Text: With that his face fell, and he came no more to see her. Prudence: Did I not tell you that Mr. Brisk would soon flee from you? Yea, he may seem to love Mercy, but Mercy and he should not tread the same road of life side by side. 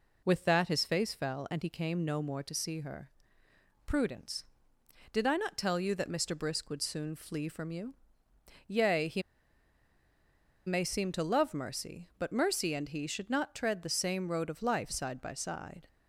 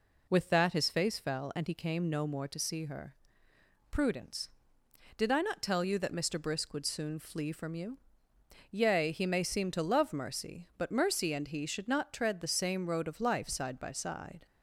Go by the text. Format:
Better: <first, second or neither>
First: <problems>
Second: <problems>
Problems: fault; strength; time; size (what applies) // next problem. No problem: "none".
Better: second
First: pauses between "he" and "may"; strong; at 9.2 s; 1.4 s long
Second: none